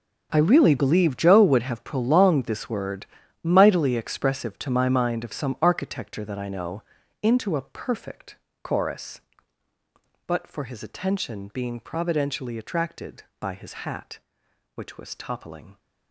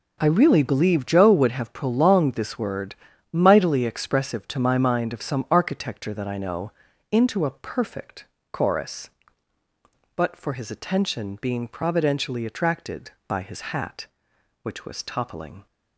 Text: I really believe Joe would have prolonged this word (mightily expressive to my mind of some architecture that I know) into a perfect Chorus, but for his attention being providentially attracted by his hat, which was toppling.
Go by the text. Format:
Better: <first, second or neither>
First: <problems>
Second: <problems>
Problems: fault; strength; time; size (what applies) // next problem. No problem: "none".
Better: second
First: gets quieter; strong; throughout; 15 dB // pauses between "perfect" and "Chorus"; slight; at 8.3 s; 0.26 s long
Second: pauses between "perfect" and "Chorus"; slight; at 8.2 s; 0.26 s long